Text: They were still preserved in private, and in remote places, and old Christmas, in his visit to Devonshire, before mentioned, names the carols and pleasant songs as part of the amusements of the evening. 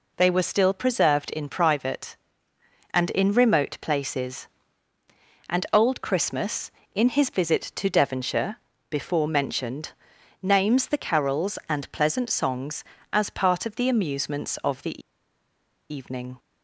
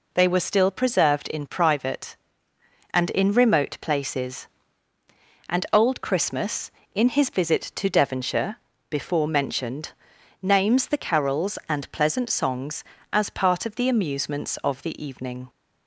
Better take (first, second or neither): second